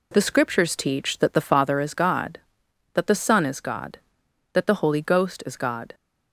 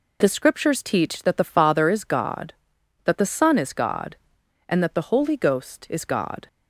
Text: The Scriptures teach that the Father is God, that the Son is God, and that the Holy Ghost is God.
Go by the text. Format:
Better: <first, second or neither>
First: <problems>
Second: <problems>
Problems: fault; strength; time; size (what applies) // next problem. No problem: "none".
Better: second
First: skips "and"; at 4.2 s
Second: none